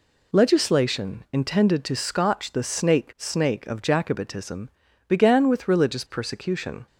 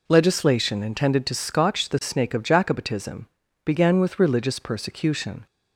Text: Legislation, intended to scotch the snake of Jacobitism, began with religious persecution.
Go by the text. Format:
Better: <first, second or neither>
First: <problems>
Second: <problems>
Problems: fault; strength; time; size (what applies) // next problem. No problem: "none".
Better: second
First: says "snake" twice; at 3.1 s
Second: none